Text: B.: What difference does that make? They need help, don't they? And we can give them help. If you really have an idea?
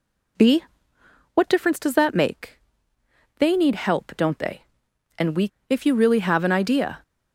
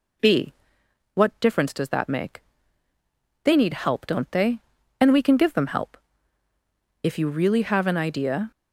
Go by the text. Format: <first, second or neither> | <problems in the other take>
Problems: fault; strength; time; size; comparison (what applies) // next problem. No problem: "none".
second | skips "can give them help"; at 5.5 s